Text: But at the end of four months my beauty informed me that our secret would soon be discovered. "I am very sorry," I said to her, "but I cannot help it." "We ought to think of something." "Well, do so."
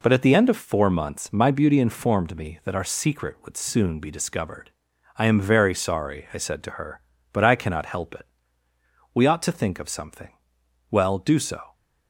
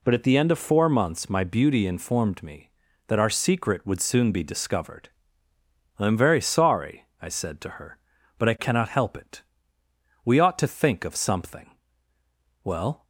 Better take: first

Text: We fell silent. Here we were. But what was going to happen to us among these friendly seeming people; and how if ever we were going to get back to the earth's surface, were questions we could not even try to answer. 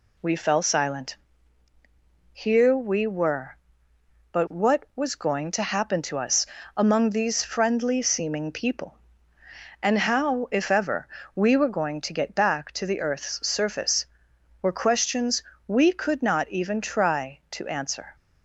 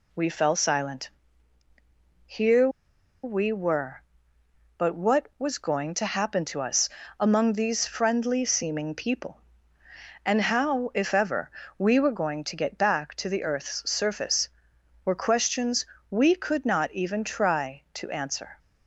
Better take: first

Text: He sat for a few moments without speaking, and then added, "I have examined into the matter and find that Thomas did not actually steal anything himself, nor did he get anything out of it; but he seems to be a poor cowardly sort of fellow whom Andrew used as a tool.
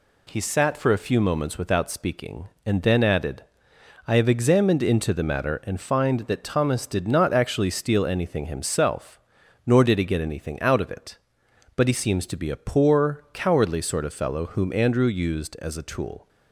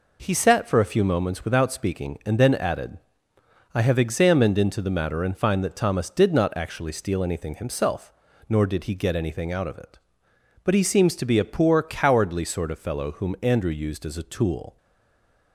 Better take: first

